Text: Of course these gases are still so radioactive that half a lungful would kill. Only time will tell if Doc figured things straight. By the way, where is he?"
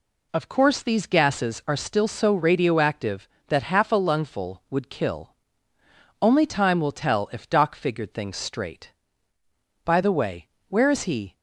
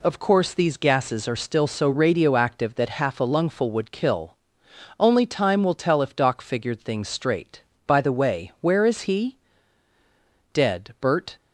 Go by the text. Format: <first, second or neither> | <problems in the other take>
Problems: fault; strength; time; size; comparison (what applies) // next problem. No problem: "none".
first | goes on to say "Dead Bert"; noticeable; from 10.5 s on; 0.82 s long